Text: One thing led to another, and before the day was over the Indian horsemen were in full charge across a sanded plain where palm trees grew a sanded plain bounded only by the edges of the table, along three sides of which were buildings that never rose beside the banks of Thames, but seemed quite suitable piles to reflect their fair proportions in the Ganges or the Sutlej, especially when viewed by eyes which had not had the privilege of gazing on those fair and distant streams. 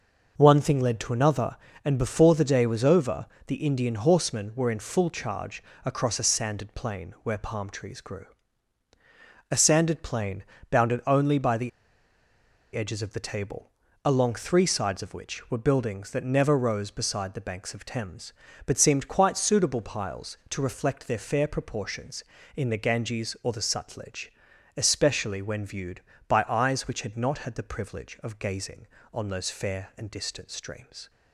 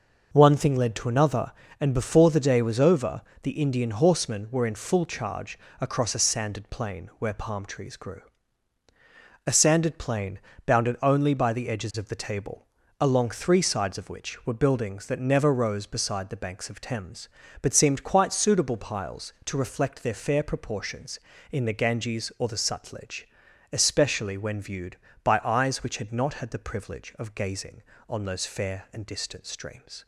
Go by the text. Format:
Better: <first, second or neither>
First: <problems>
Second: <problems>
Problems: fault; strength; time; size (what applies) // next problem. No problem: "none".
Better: second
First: pauses between "over" and "the"; slight; at 3.2 s; 0.22 s long // pauses between "charge" and "across"; slight; at 5.6 s; 0.20 s long // pauses between "grew" and "a"; at 8.2 s; 1.2 s long // pauses between "plain" and "bounded"; slight; at 10.4 s; 0.26 s long // pauses between "the" and "edges"; at 11.6 s; 1.0 s long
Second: pauses between "over" and "the"; slight; at 3.2 s; 0.22 s long // pauses between "charge" and "across"; slight; at 5.5 s; 0.20 s long // pauses between "grew" and "a"; at 8.2 s; 1.2 s long // pauses between "plain" and "bounded"; slight; at 10.3 s; 0.26 s long